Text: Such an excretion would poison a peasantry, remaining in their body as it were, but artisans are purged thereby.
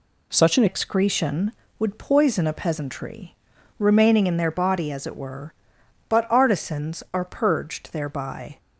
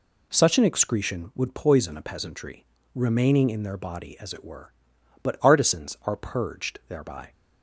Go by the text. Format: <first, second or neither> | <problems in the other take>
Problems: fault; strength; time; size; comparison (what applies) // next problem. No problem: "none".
second | changes voice at "excretion"; from 0.6 s on; 7.9 s long